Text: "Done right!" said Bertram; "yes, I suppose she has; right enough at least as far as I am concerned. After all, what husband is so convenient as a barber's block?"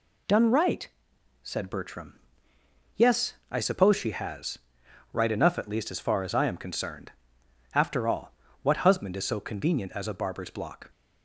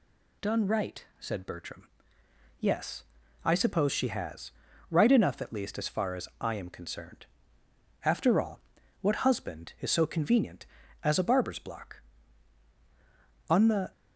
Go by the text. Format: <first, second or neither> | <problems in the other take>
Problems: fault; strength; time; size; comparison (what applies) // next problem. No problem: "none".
first | goes on to say "On the"; slight; from 13.4 s on; 0.42 s long